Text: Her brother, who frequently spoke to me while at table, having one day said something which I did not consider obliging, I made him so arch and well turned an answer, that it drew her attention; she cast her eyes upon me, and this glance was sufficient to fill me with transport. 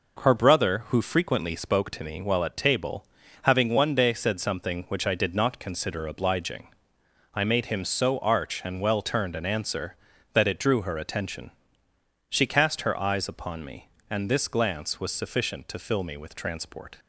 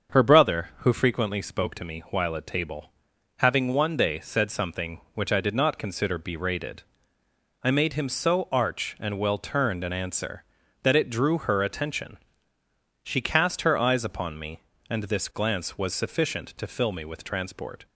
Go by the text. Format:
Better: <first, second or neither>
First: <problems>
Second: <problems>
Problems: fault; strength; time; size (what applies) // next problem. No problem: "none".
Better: first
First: none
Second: starts louder than the rest; until 1.1 s; 6.5 dB // says "berated" for "obliging"; at 6.1 s